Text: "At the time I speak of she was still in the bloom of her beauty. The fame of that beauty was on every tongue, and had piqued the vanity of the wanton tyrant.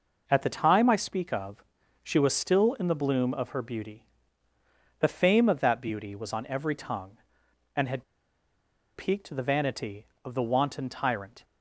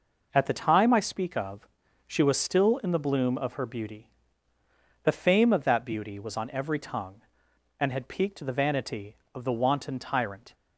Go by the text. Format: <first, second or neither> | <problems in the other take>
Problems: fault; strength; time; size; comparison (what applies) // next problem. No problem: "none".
second | pauses between "of" and "she"; at 1.6 s; 0.38 s long; also in the second // pauses between "had" and "piqued"; noticeable; at 8.0 s; 0.92 s long